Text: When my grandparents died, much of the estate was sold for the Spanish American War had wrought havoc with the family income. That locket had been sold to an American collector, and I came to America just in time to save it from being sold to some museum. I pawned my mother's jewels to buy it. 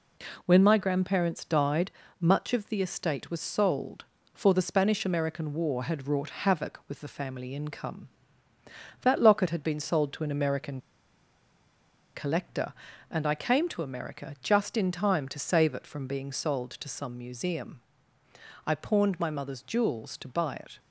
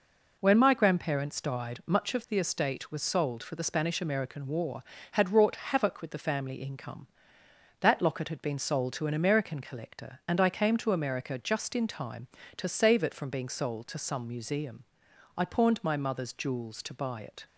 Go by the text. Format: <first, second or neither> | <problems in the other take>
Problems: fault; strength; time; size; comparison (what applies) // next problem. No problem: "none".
second | pauses between "American" and "collector"; strong; at 10.8 s; 1.3 s long